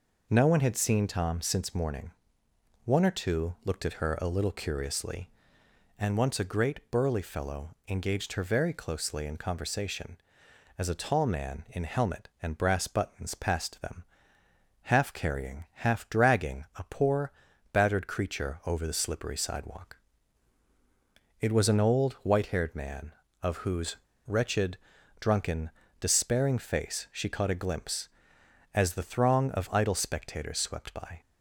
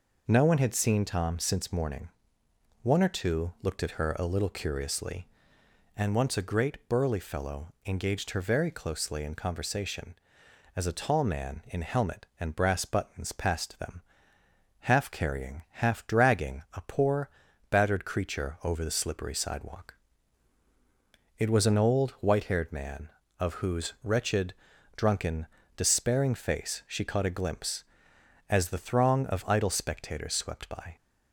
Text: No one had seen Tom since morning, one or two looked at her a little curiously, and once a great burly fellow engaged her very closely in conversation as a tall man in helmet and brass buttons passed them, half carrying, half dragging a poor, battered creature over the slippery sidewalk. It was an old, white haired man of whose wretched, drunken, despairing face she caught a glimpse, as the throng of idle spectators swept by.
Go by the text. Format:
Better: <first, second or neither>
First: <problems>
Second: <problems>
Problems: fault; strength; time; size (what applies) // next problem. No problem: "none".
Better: second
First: pauses between "whose" and "wretched"; slight; at 23.9 s; 0.32 s long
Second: none